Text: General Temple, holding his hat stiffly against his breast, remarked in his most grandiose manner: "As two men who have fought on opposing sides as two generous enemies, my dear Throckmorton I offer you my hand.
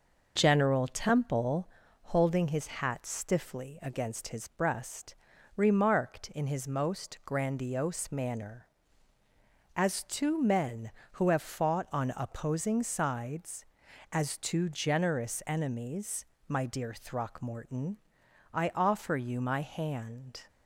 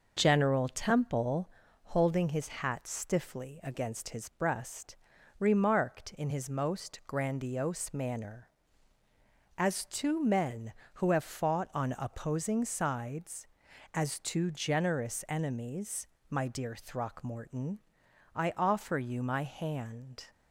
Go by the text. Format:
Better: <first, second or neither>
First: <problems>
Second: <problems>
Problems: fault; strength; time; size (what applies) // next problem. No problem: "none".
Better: neither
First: pauses between "Throckmorton" and "I"; noticeable; at 17.9 s; 0.54 s long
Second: pauses between "Throckmorton" and "I"; noticeable; at 17.8 s; 0.54 s long